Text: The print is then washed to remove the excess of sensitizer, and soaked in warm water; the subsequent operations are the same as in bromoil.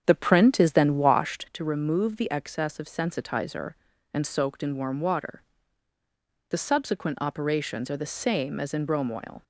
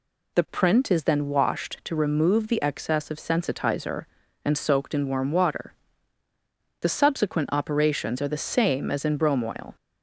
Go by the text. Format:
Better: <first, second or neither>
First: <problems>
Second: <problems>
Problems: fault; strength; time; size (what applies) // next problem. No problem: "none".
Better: second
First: starts louder than the rest; strong; until 1.5 s; 8 dB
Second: none